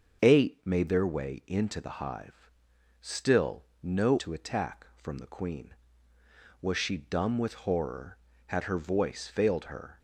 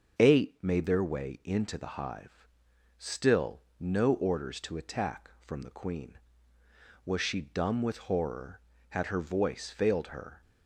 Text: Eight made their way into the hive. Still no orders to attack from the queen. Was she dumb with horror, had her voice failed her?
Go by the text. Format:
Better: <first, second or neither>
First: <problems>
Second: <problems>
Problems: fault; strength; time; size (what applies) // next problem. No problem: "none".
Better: second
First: starts louder than the rest; until 1.2 s; 6 dB // pauses between "Still" and "no"; slight; at 3.6 s; 0.18 s long // skips "orders"; at 4.1 s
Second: starts louder than the rest; noticeable; until 1.2 s; 6 dB // pauses between "Still" and "no"; slight; at 3.6 s; 0.18 s long